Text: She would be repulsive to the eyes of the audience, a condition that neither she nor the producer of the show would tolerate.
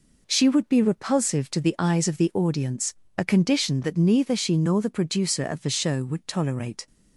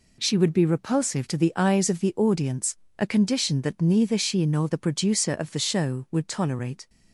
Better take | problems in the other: neither | none

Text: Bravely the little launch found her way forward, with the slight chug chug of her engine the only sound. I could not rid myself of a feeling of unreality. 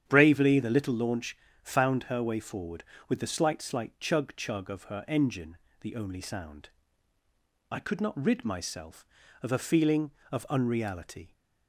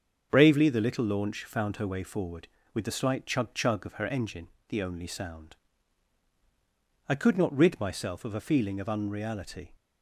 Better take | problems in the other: second | starts louder than the rest; strong; until 1.0 s; 9.5 dB; also in the second // pauses between "launch" and "found"; slight; at 1.3 s; 0.26 s long // says "slight" twice; at 3.6 s // pauses between "engine" and "the"; slight; at 5.5 s; 0.24 s long; slight in the second

